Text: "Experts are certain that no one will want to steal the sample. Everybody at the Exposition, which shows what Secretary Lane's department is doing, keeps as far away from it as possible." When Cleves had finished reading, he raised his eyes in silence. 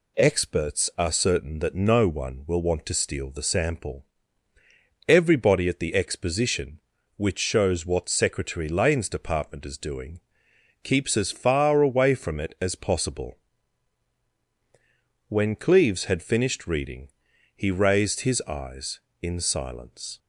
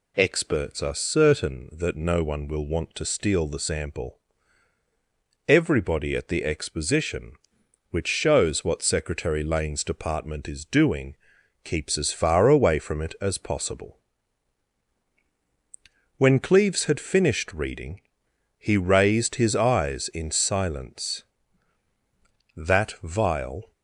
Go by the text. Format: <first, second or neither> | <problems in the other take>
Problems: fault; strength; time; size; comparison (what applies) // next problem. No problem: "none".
first | goes on to say "That vial"; noticeable; from 22.5 s on; 1.1 s long